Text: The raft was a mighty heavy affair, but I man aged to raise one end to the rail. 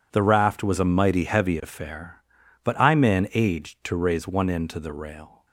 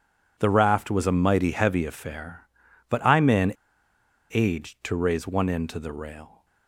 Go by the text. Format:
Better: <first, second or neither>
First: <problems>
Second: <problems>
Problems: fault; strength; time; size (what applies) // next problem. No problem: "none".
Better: first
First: none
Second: pauses between "man" and "aged"; noticeable; at 3.5 s; 0.82 s long